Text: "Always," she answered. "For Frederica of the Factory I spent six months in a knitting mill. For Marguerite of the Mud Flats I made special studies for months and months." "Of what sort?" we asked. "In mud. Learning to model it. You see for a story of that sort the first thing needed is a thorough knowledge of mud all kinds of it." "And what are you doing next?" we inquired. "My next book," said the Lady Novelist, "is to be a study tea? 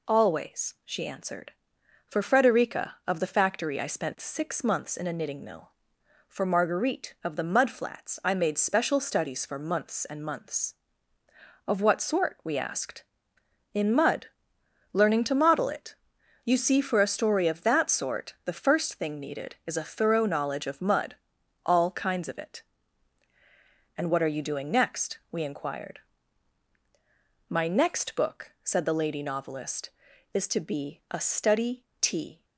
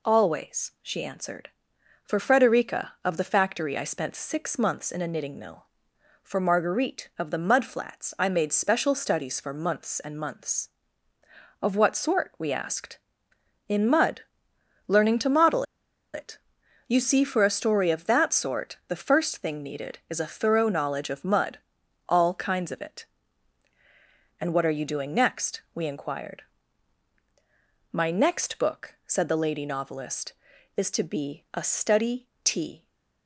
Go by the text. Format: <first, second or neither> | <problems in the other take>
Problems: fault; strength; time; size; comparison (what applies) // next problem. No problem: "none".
first | pauses between "model" and "it"; noticeable; at 15.6 s; 0.50 s long // pauses between "mud" and "all"; noticeable; at 21.5 s; 0.50 s long; noticeable in the first // pauses between "study" and "tea"; slight; at 32.2 s; 0.18 s long; slight in the first